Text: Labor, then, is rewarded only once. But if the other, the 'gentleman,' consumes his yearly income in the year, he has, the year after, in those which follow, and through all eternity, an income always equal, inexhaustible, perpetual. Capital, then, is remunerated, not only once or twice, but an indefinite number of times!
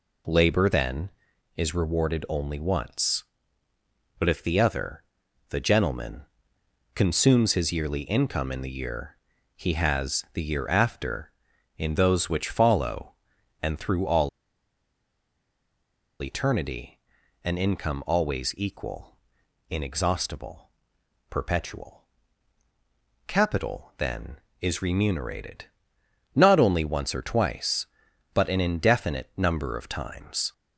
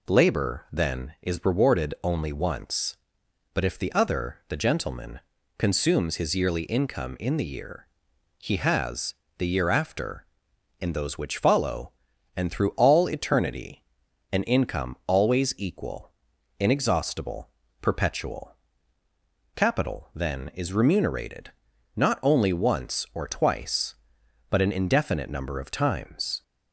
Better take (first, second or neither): second